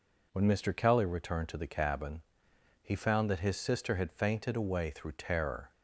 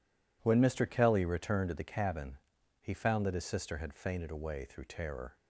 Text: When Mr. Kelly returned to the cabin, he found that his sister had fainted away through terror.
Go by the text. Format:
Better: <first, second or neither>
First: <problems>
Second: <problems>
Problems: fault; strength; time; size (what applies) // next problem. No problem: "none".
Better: neither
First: none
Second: none